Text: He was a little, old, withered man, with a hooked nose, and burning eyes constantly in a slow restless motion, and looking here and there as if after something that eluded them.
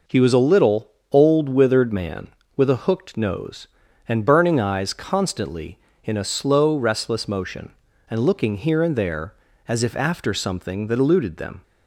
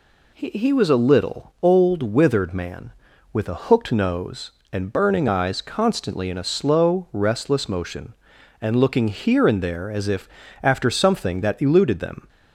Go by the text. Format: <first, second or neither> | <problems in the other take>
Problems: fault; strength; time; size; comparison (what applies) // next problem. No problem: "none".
first | says "He" twice; at 0.4 s // pauses between "if" and "after"; slight; at 10.3 s; 0.32 s long